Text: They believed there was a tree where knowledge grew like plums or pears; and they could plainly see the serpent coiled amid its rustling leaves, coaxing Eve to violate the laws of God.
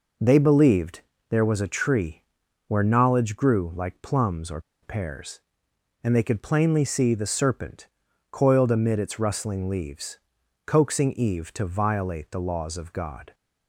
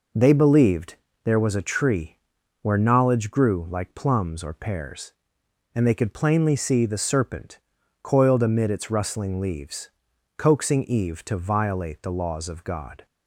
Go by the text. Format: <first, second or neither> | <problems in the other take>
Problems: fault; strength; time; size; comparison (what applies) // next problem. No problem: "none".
second | pauses between "believed" and "there"; slight; at 1.0 s; 0.28 s long; slight in the second // pauses between "tree" and "where"; at 2.2 s; 0.42 s long; also in the second // pauses between "or" and "pears"; slight; at 4.5 s; 0.23 s long // pauses between "serpent" and "coiled"; at 7.8 s; 0.42 s long; also in the second